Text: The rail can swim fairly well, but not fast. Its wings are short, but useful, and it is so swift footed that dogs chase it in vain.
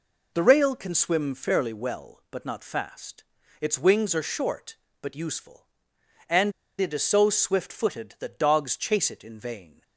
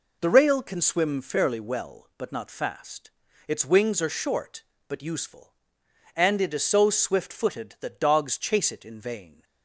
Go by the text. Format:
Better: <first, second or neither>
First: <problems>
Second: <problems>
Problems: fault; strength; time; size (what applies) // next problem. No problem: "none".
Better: second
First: pauses between "and" and "it"; slight; at 6.5 s; 0.28 s long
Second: none